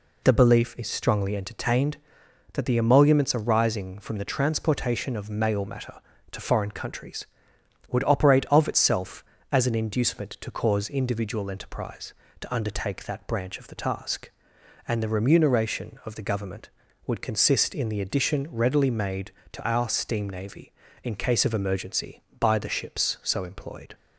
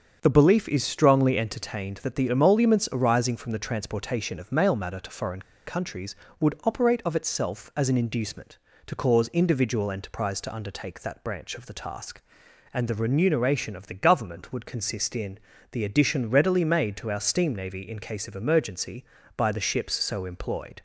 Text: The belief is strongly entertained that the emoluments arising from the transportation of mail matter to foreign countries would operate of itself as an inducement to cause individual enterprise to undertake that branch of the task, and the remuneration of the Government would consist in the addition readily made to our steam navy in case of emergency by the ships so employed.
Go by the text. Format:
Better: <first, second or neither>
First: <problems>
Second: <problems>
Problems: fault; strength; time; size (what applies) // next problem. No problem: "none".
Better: first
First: none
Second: starts louder than the rest; strong; until 1.2 s; 7 dB // pauses between "foreign" and "countries"; slight; at 5.4 s; 0.23 s long // pauses between "in" and "the"; slight; at 15.4 s; 0.32 s long